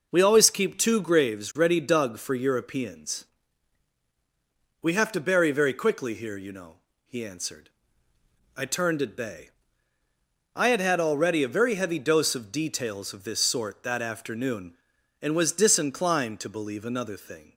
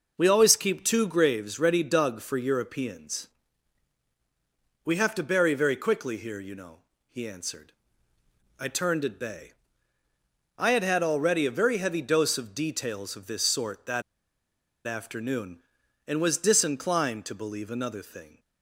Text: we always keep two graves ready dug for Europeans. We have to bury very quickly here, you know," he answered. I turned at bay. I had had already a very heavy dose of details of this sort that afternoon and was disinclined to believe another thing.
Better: first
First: none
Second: pauses between "that" and "afternoon"; noticeable; at 14.0 s; 0.85 s long

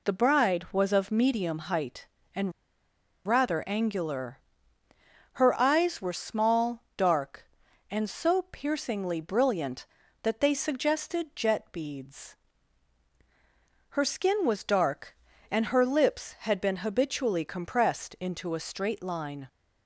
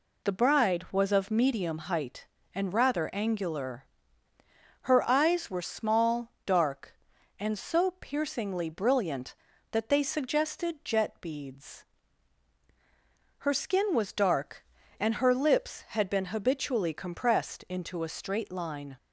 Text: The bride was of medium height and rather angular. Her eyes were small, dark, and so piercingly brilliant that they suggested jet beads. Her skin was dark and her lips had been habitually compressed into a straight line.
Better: second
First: pauses between "and" and "rather"; noticeable; at 2.5 s; 0.74 s long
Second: none

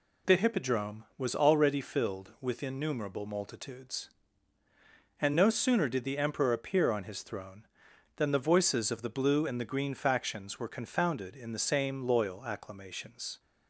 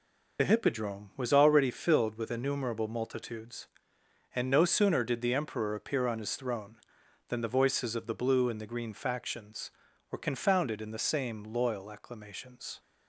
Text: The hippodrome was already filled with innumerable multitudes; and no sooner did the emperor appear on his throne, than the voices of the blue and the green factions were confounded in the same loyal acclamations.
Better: first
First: none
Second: loses the start of "The"; at 0.3 s; 50 ms

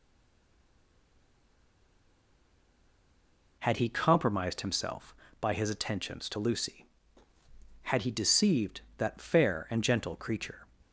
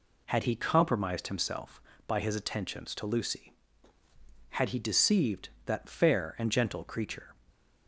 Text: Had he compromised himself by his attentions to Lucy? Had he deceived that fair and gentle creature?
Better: second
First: stays silent before the first word; strong; until 3.5 s; 3.5 s long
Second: none

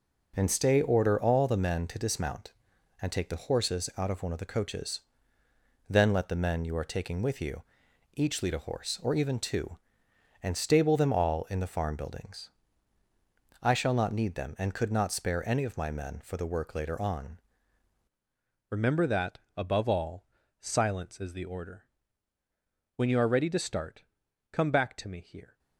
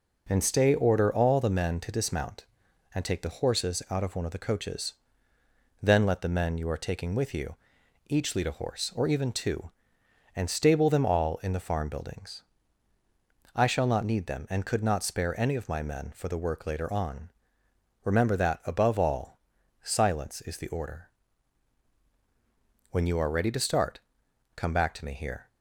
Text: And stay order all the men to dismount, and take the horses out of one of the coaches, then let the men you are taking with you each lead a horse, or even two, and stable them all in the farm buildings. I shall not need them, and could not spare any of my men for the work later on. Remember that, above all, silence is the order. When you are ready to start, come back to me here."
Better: second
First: pauses between "you" and "each"; noticeable; at 7.6 s; 0.52 s long // changes voice at "Remember"; from 18.6 s on; 6.9 s long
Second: pauses between "you" and "each"; noticeable; at 7.5 s; 0.52 s long

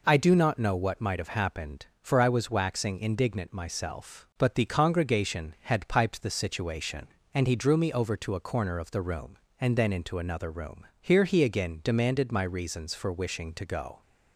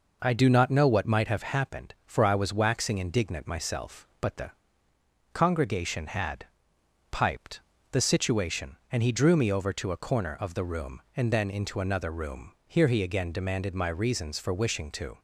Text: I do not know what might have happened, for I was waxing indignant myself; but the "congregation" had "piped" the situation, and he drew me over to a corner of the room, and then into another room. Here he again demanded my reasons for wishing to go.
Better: first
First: none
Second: pauses between "the" and "congregation"; noticeable; at 4.5 s; 0.80 s long // pauses between "had" and "piped"; noticeable; at 6.4 s; 0.64 s long // pauses between "piped" and "the"; slight; at 7.6 s; 0.30 s long // stops before "go"; at 15.1 s

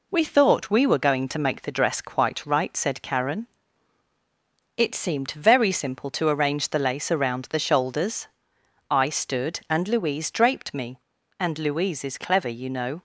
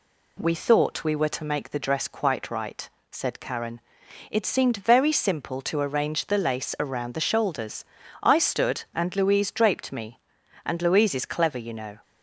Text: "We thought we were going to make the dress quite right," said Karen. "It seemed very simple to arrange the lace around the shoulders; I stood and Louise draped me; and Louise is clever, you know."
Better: first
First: none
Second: skips "going"; at 1.3 s

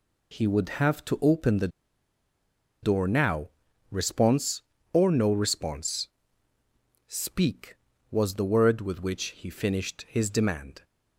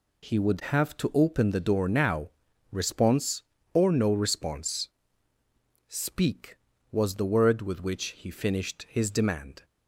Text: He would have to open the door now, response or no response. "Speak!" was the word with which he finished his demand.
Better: second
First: pauses between "the" and "door"; at 1.6 s; 1.1 s long // pauses between "which" and "he"; slight; at 9.2 s; 0.18 s long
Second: pauses between "which" and "he"; slight; at 8.0 s; 0.18 s long

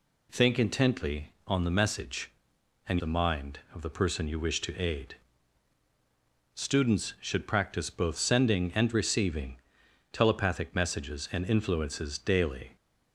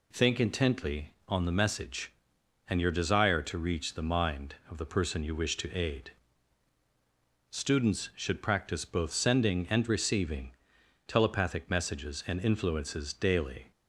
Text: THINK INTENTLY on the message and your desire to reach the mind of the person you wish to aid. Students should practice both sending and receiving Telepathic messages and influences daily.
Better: second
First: skips "your desire to reach"; at 2.9 s // pauses between "receiving" and "Telepathic"; noticeable; at 9.5 s; 0.56 s long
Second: pauses between "receiving" and "Telepathic"; noticeable; at 10.5 s; 0.56 s long

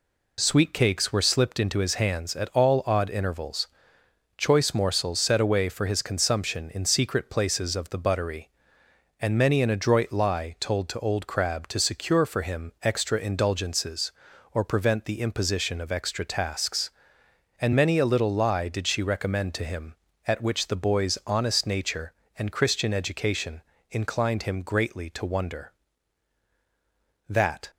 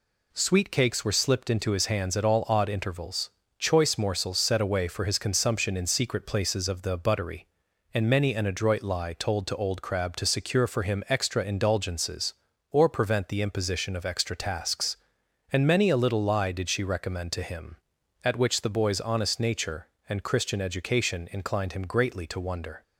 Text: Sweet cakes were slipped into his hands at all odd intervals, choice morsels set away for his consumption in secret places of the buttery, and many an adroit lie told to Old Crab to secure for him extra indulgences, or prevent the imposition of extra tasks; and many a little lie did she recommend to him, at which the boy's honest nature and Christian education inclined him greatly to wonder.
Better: second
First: pauses between "education" and "inclined"; slight; at 23.6 s; 0.28 s long // goes on to say "That"; slight; from 27.2 s on; 0.44 s long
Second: none

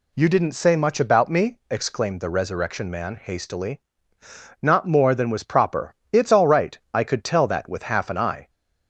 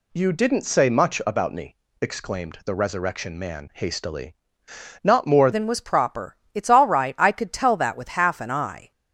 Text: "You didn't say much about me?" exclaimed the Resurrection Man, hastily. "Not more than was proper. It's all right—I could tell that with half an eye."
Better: first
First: none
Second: changes voice at "than"; from 5.5 s on; 3.4 s long

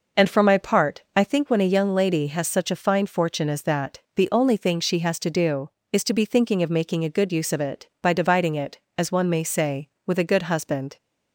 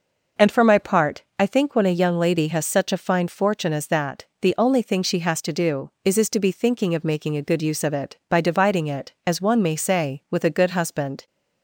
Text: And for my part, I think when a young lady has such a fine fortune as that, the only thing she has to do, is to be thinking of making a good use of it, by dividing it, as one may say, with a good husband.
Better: first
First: none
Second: says "is" twice; at 6.1 s

